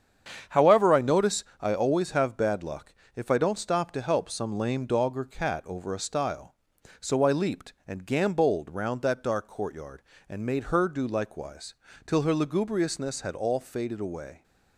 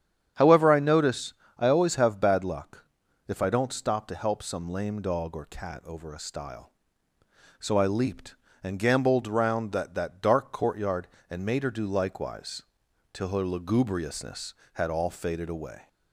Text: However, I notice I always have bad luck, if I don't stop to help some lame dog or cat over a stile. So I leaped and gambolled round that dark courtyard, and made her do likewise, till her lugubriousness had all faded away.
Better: first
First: starts louder than the rest; strong; until 1.6 s; 8 dB // pauses between "notice" and "I"; slight; at 1.4 s; 0.18 s long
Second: starts louder than the rest; strong; until 1.6 s; 9 dB // pauses between "notice" and "I"; slight; at 1.3 s; 0.24 s long // says "that" twice; at 9.9 s

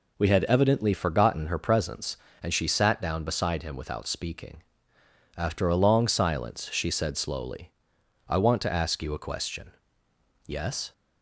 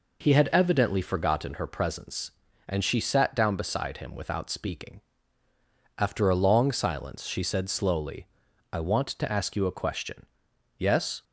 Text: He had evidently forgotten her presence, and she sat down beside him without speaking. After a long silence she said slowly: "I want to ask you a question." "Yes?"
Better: second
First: says "We" for "He"; at 0.1 s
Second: none

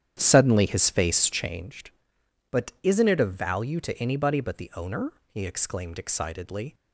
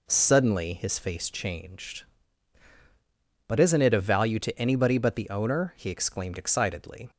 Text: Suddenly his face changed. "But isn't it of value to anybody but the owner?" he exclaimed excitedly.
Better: second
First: starts louder than the rest; strong; until 1.7 s; 9.5 dB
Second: none

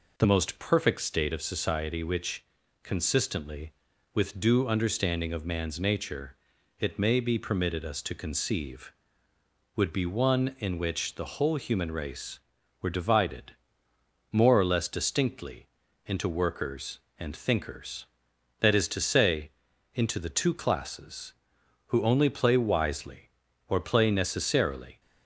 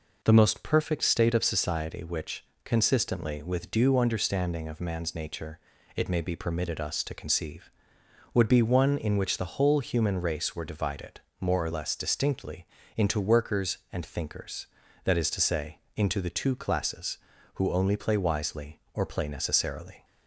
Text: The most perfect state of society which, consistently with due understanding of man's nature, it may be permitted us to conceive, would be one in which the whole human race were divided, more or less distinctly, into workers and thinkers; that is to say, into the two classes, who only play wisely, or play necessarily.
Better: second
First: changes voice at "most"; from 0.2 s on; 24.7 s long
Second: none

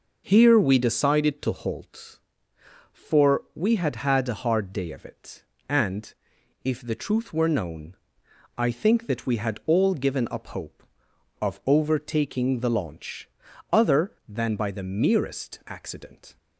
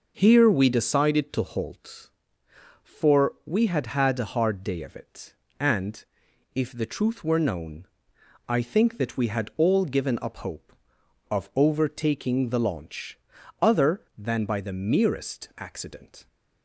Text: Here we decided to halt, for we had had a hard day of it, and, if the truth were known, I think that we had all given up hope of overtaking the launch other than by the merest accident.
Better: neither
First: pauses between "launch" and "other"; at 13.2 s; 0.42 s long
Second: pauses between "launch" and "other"; at 13.1 s; 0.42 s long

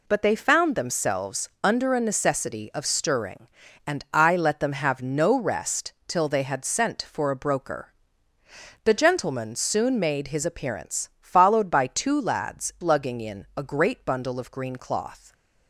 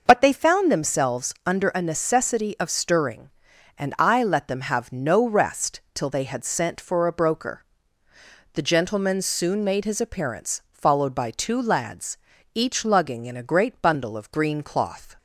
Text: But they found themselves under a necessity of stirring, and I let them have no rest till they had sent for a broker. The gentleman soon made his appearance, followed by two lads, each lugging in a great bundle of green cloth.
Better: second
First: skips "each"; at 12.7 s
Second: none

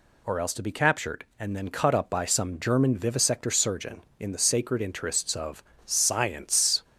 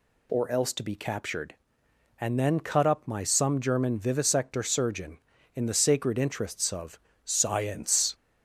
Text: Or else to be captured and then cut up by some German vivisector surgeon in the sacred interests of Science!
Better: first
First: pauses between "of" and "Science"; slight; at 5.6 s; 0.22 s long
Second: says "my" for "by"; at 3.0 s // pauses between "of" and "Science"; slight; at 7.0 s; 0.24 s long

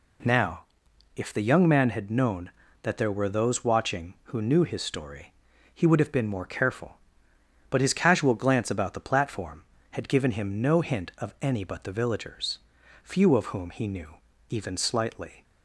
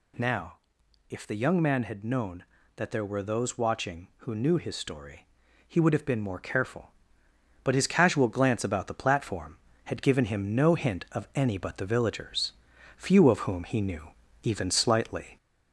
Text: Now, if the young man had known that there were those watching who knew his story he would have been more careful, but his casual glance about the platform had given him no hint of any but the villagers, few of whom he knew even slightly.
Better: first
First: pauses between "story" and "he"; at 5.3 s; 0.40 s long // pauses between "knew" and "even"; slight; at 14.1 s; 0.34 s long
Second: gets louder; slight; throughout; 3 dB // pauses between "story" and "he"; at 5.2 s; 0.40 s long // pauses between "knew" and "even"; slight; at 14.1 s; 0.34 s long

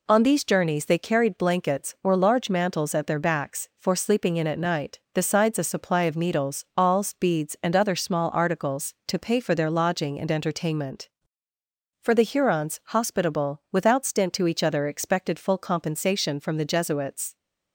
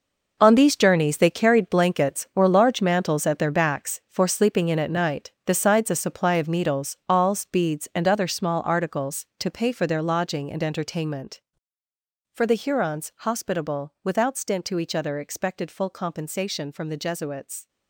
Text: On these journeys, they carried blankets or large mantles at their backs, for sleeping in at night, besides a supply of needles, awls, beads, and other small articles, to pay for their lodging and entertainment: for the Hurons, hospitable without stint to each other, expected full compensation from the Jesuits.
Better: first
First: none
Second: gets quieter; strong; throughout; 12 dB

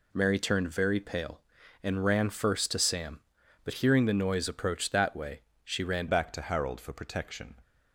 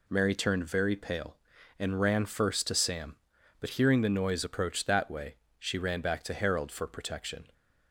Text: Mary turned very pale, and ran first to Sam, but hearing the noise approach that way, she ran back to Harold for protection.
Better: second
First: changes voice at "back"; from 6.0 s on; 1.5 s long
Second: none

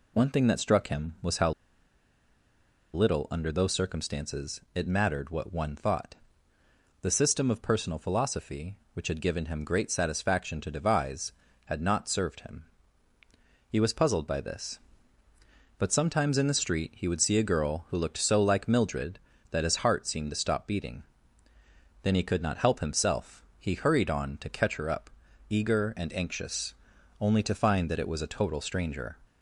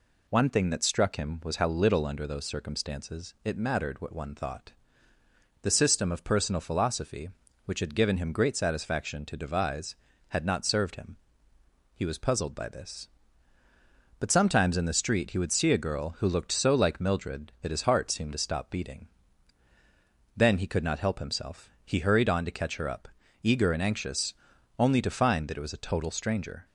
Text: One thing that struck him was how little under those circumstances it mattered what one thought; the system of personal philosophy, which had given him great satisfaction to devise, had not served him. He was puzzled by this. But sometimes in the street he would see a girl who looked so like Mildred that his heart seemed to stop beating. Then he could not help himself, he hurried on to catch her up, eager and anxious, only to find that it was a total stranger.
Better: second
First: pauses between "how" and "little"; strong; at 1.5 s; 1.4 s long // pauses between "circumstances" and "it"; slight; at 4.5 s; 0.16 s long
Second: none

